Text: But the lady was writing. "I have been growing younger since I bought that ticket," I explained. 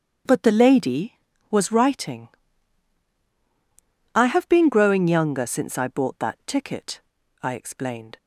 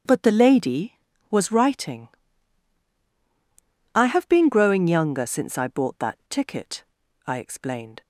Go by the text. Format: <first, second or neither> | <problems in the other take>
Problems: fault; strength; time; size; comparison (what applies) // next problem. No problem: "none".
neither | starts louder than the rest; strong; the same in both